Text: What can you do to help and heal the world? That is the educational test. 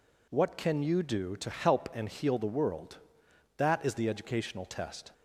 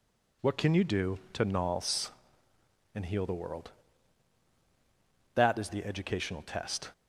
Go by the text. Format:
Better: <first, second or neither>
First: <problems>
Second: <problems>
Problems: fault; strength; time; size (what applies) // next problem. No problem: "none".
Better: first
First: none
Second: says "nals" for "help"; at 1.4 s